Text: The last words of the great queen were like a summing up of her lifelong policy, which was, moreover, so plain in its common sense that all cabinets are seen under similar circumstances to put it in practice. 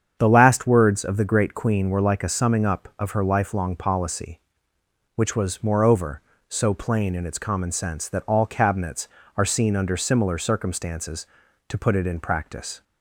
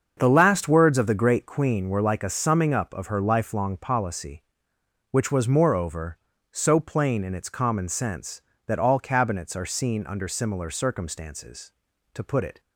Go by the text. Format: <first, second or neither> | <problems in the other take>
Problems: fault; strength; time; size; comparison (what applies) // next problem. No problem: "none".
first | starts louder than the rest; until 1.1 s; 6.5 dB; strong in the first // stops before "in practice"; at 12.6 s